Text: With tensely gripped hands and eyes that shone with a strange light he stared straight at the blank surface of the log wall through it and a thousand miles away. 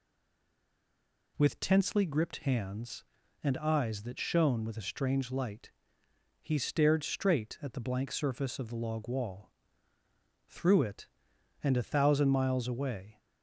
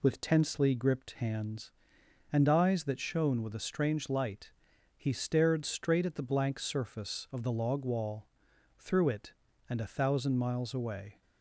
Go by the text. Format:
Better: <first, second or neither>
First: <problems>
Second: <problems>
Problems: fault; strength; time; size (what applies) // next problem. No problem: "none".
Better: second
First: stays silent before the first word; noticeable; until 1.3 s; 1.3 s long // pauses between "light" and "he"; noticeable; at 5.7 s; 0.70 s long // pauses between "wall" and "through"; noticeable; at 9.5 s; 0.96 s long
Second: pauses between "light" and "he"; noticeable; at 4.5 s; 0.46 s long // pauses between "wall" and "through"; noticeable; at 8.2 s; 0.52 s long